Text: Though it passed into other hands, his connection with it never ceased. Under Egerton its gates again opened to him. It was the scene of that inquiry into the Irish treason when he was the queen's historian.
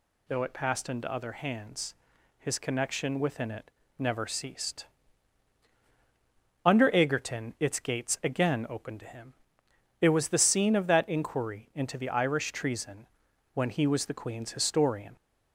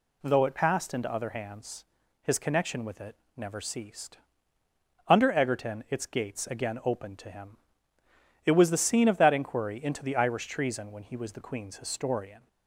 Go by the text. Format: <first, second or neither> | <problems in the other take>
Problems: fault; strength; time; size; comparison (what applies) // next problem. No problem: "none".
second | says "within" for "with"; at 3.1 s // pauses between "it" and "never"; slight; at 3.7 s; 0.28 s long; slight in the second // pauses between "treason" and "when"; noticeable; at 13.0 s; 0.46 s long